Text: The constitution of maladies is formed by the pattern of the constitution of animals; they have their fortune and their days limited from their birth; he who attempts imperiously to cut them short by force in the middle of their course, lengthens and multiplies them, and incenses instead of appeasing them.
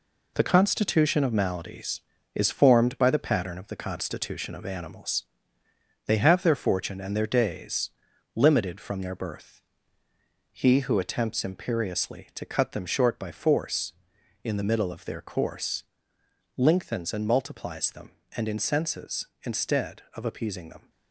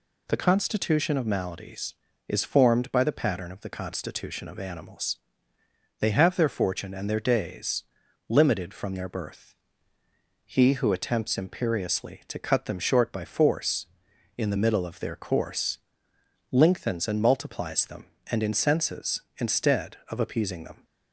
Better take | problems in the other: second | gets quieter; noticeable; throughout; 6 dB // pauses between "days" and "limited"; at 7.9 s; 0.42 s long; also in the second

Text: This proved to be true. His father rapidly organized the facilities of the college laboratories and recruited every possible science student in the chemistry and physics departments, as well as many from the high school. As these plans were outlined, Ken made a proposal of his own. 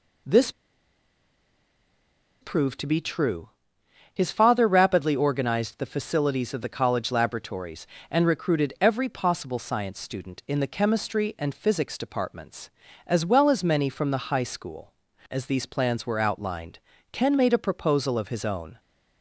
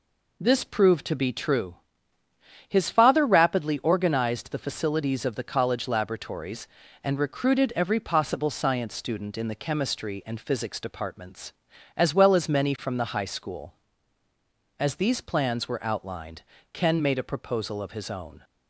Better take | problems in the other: second | pauses between "This" and "proved"; strong; at 0.5 s; 1.8 s long

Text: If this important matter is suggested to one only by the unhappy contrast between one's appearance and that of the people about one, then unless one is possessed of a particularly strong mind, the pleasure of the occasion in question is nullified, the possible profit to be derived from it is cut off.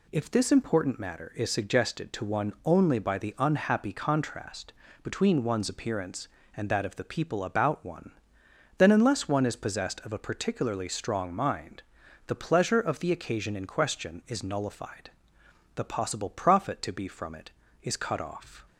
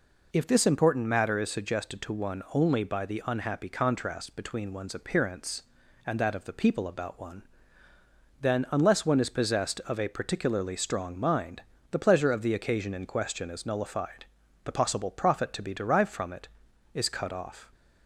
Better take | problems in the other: second | pauses between "contrast" and "between"; slight; at 4.7 s; 0.32 s long // skips "derived"; at 17.0 s

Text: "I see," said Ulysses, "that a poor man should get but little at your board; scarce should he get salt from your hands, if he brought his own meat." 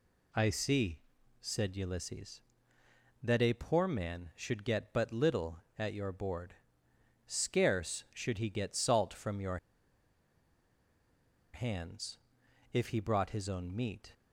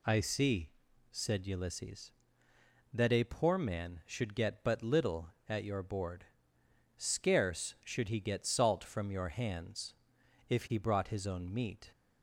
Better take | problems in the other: second | pauses between "your" and "hands"; strong; at 9.5 s; 1.9 s long

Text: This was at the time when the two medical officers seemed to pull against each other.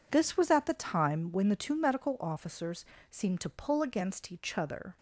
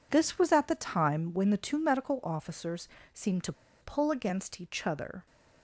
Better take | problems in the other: first | pauses between "officers" and "seemed"; slight; at 2.8 s; 0.26 s long; slight in the first // pauses between "to" and "pull"; slight; at 3.5 s; 0.28 s long

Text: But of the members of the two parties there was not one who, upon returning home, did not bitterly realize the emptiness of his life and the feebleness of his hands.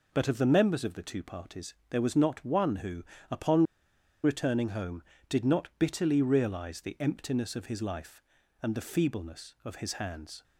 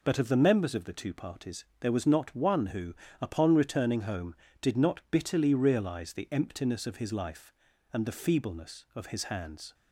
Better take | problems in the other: second | pauses between "parties" and "there"; slight; at 1.7 s; 0.18 s long; slight in the second // pauses between "upon" and "returning"; noticeable; at 3.6 s; 0.61 s long

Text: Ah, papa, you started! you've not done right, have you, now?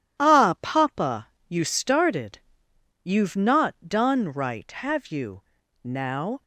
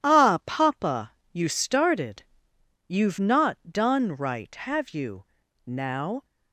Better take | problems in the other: neither | pauses between "not" and "done"; slight; the same in both

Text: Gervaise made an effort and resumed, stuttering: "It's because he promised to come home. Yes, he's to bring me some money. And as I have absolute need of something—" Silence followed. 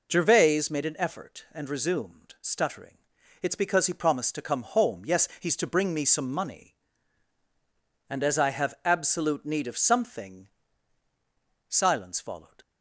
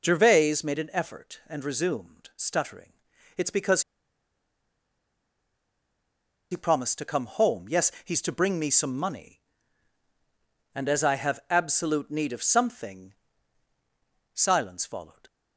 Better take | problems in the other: first | pauses between "because" and "he"; strong; at 3.8 s; 2.6 s long

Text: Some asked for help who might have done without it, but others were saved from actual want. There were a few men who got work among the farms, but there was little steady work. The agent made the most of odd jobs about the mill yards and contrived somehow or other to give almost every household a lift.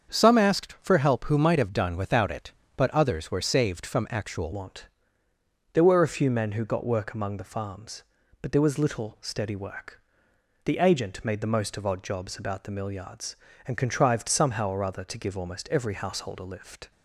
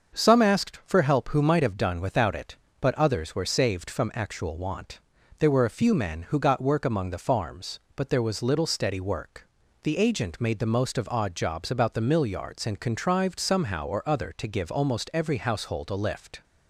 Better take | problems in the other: second | starts louder than the rest; strong; until 1.1 s; 7 dB; also in the second // changes voice at "want"; from 4.5 s on; 12.4 s long

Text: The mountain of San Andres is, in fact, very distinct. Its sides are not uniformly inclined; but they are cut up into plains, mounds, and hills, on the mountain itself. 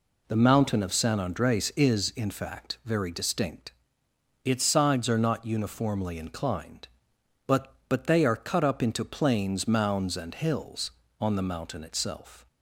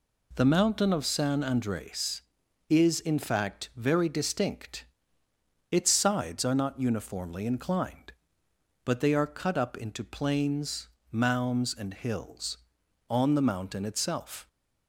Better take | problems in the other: second | says "but" twice; at 7.8 s

